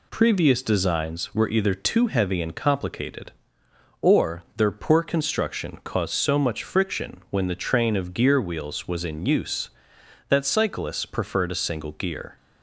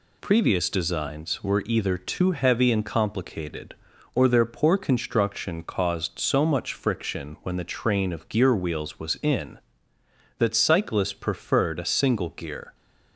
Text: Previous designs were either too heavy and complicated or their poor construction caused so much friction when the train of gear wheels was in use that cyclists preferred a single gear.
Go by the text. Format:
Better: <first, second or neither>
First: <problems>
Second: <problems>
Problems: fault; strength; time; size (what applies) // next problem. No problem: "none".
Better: first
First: none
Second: skips "use"; at 9.9 s